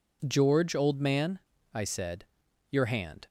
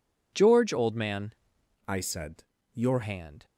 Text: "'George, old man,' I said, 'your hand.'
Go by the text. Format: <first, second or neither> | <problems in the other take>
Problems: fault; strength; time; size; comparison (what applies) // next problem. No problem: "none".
first | changes voice from "I" to "your"; from 1.8 to 3.0 s; 1.2 s long